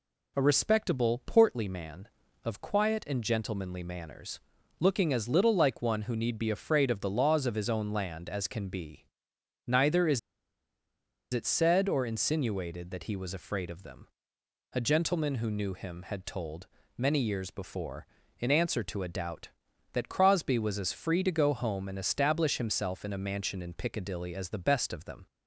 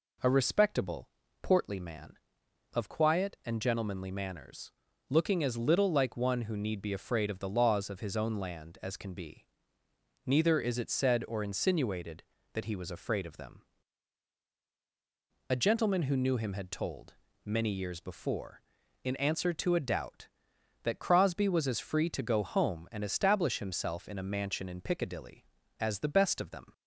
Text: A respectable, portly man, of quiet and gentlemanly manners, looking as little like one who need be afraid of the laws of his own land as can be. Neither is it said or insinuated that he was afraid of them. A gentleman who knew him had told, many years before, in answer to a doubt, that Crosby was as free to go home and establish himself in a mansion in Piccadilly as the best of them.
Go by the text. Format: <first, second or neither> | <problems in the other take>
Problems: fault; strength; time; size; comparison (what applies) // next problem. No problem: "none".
second | pauses between "is" and "it"; at 10.1 s; 1.1 s long